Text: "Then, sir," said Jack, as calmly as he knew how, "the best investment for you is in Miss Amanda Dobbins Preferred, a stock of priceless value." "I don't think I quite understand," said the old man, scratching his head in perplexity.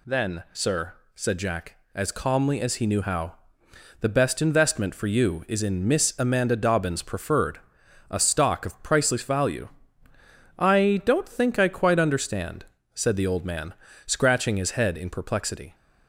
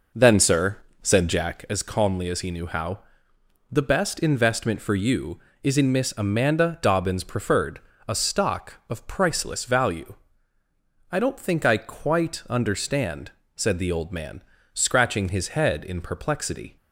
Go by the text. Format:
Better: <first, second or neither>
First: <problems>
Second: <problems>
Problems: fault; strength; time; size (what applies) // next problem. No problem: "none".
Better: first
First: none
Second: starts louder than the rest; noticeable; until 1.8 s; 5 dB